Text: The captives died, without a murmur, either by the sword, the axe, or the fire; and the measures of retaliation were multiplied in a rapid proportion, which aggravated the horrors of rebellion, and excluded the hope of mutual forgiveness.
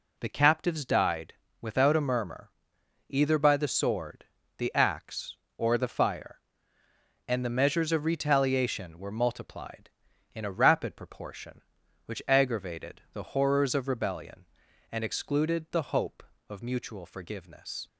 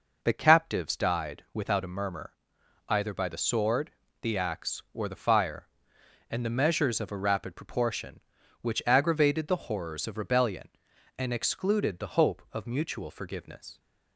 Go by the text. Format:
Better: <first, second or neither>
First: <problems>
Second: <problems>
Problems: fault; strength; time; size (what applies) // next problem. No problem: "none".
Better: first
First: none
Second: skips "retaliation were multiplied in"; at 7.1 s